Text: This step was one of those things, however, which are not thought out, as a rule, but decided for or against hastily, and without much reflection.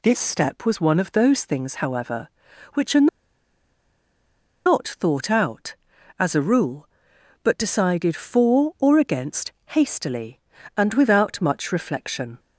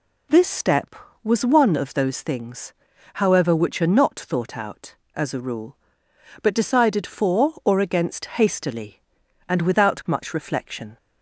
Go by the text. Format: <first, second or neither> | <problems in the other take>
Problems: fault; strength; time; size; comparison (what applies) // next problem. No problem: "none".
second | pauses between "are" and "not"; strong; at 3.0 s; 1.5 s long // pauses between "against" and "hastily"; slight; at 9.5 s; 0.16 s long